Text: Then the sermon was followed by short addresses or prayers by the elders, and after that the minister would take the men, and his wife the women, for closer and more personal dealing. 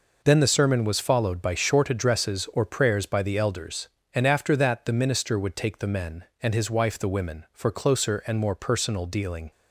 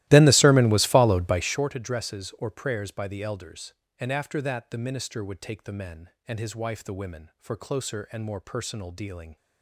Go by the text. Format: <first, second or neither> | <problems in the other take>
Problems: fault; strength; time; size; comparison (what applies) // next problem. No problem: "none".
first | starts louder than the rest; strong; until 1.6 s; 16.5 dB